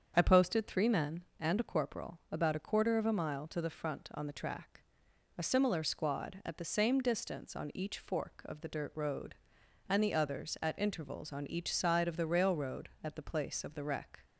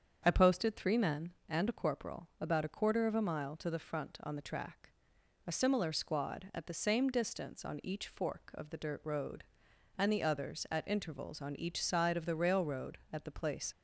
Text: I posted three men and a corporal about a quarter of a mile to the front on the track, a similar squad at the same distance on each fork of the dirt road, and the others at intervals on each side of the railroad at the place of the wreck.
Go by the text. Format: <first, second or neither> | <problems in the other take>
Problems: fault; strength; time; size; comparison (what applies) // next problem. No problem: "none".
first | starts louder than the rest; strong; until 1.2 s; 7.5 dB; strong in the first // stops before "of the wreck"; at 13.7 s